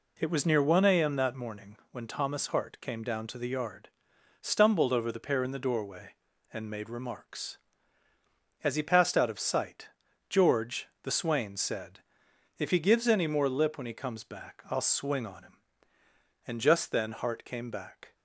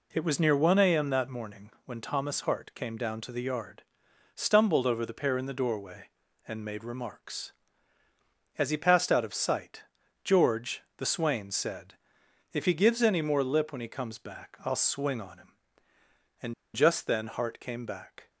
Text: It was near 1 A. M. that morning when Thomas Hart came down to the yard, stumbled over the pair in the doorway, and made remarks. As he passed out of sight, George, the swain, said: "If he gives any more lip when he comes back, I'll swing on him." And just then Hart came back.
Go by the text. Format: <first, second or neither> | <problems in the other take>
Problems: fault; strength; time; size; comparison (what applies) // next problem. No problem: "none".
first | pauses between "morning" and "when"; slight; at 1.6 s; 0.16 s long; slight in the first // pauses between "And" and "just"; slight; at 16.5 s; 0.21 s long